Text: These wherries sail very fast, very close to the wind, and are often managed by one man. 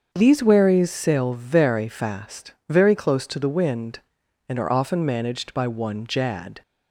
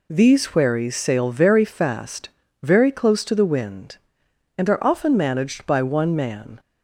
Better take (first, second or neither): second